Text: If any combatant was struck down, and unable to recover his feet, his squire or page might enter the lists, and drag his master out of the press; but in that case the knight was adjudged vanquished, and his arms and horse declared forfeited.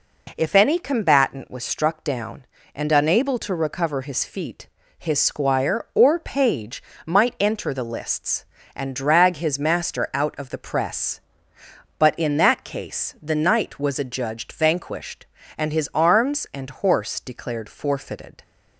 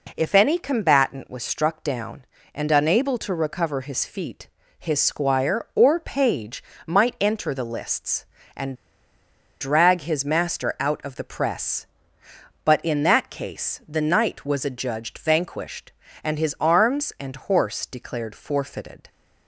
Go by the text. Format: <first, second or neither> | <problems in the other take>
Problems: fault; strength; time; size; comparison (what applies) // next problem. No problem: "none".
first | pauses between "page" and "might"; slight; at 6.6 s; 0.22 s long; slight in the first // pauses between "and" and "drag"; noticeable; at 8.7 s; 0.84 s long